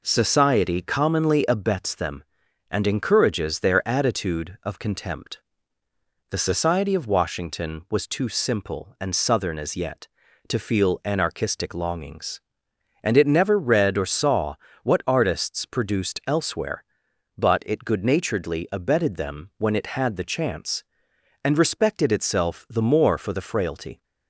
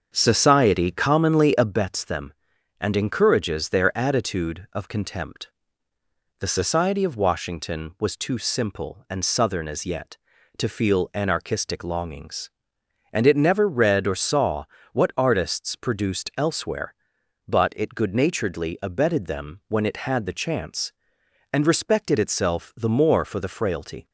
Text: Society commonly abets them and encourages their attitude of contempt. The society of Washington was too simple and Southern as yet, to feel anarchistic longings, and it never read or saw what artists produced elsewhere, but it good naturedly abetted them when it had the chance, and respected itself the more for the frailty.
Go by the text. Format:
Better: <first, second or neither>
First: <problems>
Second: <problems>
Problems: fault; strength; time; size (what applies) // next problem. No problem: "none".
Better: first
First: pauses between "saw" and "what"; slight; at 14.5 s; 0.28 s long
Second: starts louder than the rest; until 1.8 s; 7 dB // pauses between "saw" and "what"; slight; at 14.6 s; 0.28 s long